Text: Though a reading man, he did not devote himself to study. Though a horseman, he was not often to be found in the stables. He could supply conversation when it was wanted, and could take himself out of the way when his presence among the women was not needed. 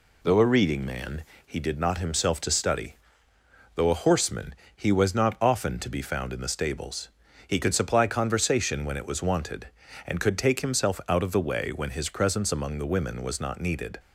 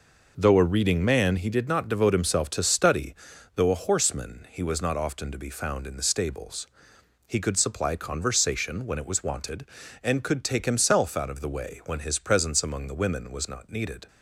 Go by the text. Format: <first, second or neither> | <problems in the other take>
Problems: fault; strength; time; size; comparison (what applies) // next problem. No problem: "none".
second | skips "devote"; at 1.9 s